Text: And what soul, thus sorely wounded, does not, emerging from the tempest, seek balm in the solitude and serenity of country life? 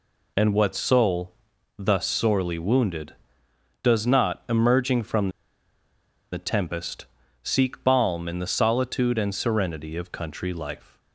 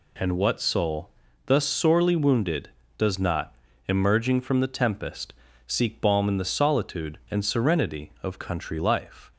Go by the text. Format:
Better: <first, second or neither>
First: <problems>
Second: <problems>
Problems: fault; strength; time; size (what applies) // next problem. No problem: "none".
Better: second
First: pauses between "from" and "the"; at 5.2 s; 1.0 s long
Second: none